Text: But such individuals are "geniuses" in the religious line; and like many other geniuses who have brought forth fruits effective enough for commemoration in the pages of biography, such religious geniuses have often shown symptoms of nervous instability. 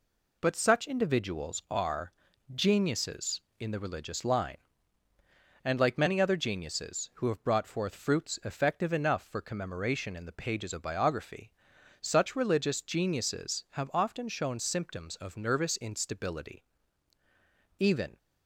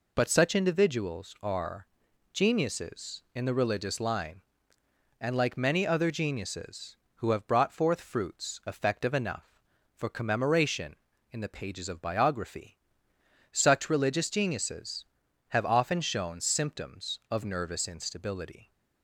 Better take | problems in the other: second | pauses between "are" and "geniuses"; at 2.1 s; 0.42 s long; noticeable in the second // goes on to say "Even"; slight; from 17.7 s on; 0.38 s long

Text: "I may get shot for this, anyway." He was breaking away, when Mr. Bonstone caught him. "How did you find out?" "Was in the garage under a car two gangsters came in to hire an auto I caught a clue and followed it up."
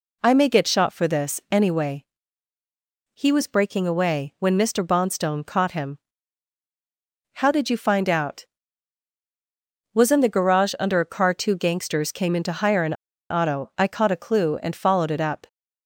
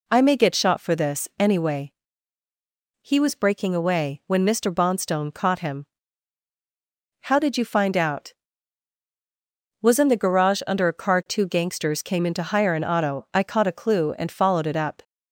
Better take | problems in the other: second | pauses between "an" and "auto"; at 12.9 s; 0.37 s long

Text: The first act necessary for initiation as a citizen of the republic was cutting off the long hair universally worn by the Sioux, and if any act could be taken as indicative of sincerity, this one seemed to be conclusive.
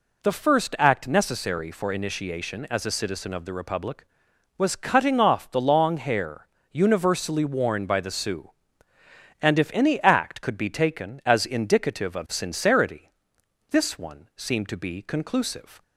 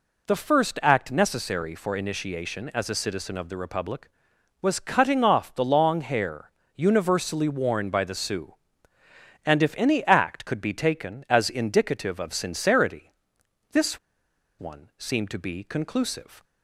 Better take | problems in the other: first | pauses between "hair" and "universally"; slight; at 6.5 s; 0.26 s long; slight in the first // pauses between "this" and "one"; noticeable; at 13.9 s; 0.60 s long

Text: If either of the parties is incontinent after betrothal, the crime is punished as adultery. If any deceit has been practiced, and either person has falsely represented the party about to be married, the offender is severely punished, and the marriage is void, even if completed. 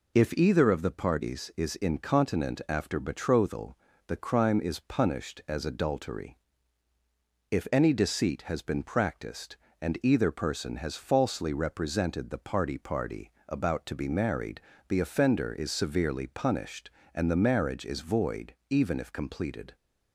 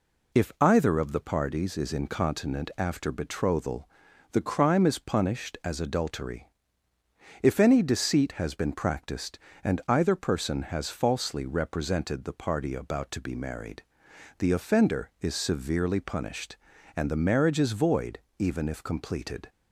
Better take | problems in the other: second | says "party" twice; at 12.7 s

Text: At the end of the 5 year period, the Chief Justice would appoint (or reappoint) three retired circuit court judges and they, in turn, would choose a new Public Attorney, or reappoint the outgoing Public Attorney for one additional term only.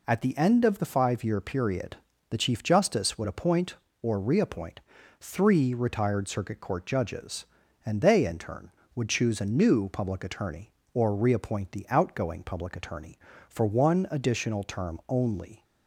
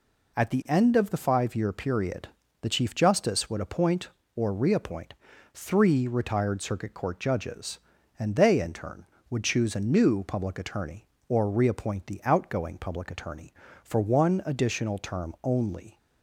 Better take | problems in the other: neither | none

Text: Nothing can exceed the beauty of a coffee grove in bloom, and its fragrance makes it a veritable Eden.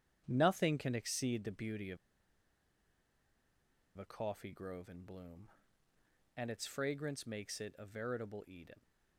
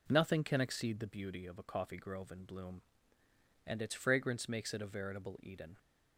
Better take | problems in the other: second | starts louder than the rest; strong; until 1.2 s; 9 dB // pauses between "of" and "a"; strong; at 1.9 s; 2.0 s long

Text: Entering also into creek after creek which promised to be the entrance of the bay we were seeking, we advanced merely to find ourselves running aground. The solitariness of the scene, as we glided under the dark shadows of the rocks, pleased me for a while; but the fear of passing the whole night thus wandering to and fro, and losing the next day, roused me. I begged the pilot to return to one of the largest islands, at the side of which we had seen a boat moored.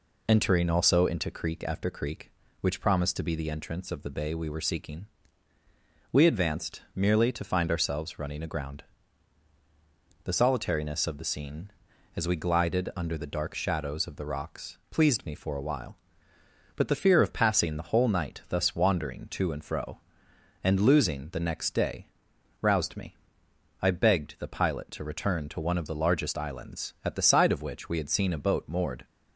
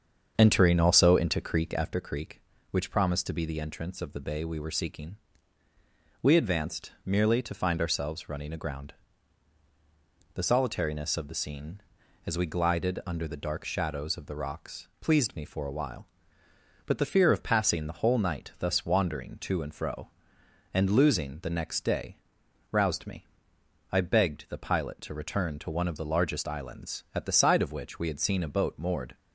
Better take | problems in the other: first | starts louder than the rest; strong; until 2.1 s; 7.5 dB

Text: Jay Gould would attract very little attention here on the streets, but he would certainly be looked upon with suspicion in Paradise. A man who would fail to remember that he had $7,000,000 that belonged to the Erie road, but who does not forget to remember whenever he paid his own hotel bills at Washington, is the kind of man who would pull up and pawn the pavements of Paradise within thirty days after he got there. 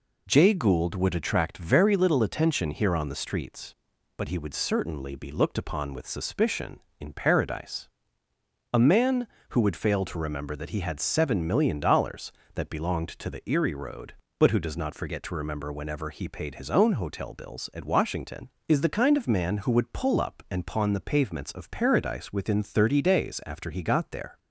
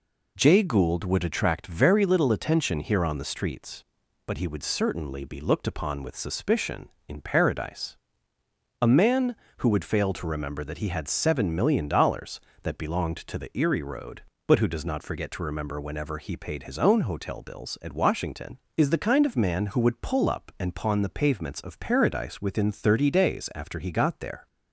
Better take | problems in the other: neither | none

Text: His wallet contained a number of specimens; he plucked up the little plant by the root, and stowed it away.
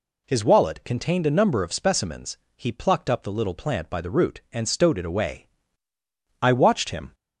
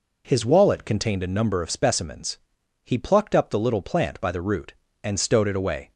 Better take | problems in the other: second | goes on to say "I watched him"; noticeable; from 6.3 s on; 0.74 s long

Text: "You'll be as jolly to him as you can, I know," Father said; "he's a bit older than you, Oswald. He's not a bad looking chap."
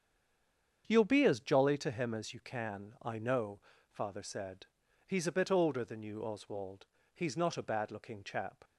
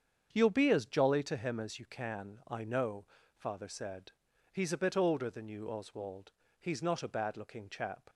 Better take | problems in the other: second | stays silent before the first word; slight; until 0.8 s; 0.8 s long // starts louder than the rest; strong; until 1.8 s; 7.5 dB; strong in the second

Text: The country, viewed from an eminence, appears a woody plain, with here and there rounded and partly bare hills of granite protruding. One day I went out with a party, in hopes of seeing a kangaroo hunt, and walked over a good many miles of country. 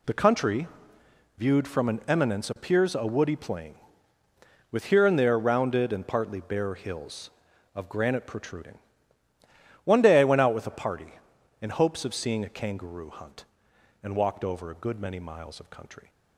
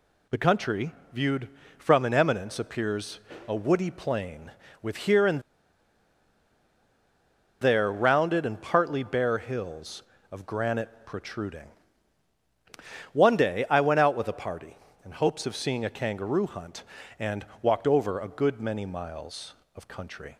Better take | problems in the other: first | pauses between "appears" and "a"; slight; at 3.1 s; 0.28 s long // pauses between "and" and "there"; strong; at 5.3 s; 2.2 s long // pauses between "and" and "walked"; slight; at 17.4 s; 0.16 s long

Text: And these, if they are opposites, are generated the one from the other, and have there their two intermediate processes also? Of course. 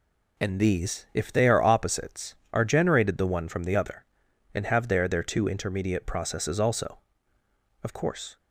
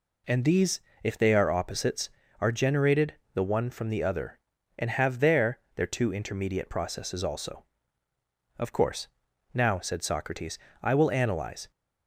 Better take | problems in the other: first | pauses between "generated" and "the"; slight; at 3.1 s; 0.20 s long // pauses between "there" and "their"; slight; at 5.5 s; 0.16 s long // goes on to say "Now said Socrates I will analyze"; strong; from 9.5 s on; 2.1 s long

